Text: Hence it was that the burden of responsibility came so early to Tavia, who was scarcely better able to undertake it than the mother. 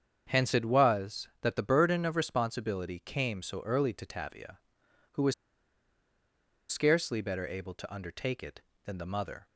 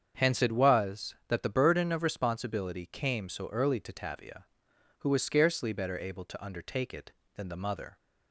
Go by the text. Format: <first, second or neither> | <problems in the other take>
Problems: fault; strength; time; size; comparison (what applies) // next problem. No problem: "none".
second | starts louder than the rest; strong; until 1.2 s; 7.5 dB; strong in the second // pauses between "was" and "scarcely"; strong; at 5.3 s; 1.3 s long